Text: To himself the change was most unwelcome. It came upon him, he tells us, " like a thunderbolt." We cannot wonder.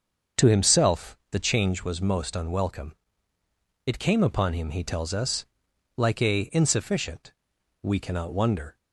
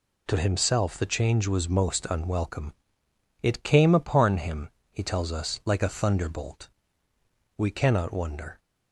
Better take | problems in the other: second | starts louder than the rest; until 1.5 s; 7 dB // says "insufficient" for "thunderbolt"; at 6.5 s

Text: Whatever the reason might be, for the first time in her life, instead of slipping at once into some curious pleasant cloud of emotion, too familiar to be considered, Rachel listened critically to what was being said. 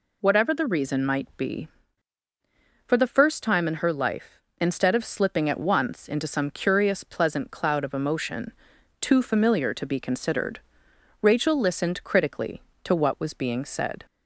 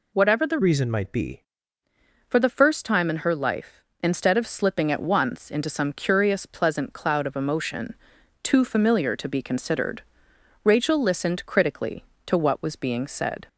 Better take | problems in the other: first | changes voice from "reason" to "be"; from 0.6 to 1.4 s; 0.8 s long

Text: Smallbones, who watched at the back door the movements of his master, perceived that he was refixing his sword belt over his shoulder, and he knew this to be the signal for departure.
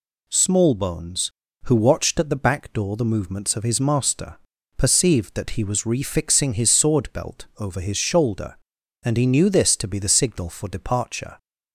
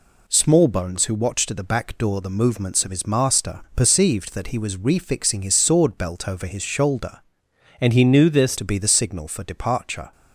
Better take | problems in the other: first | changes voice from "and" to "this"; from 7.7 to 8.5 s; 0.8 s long

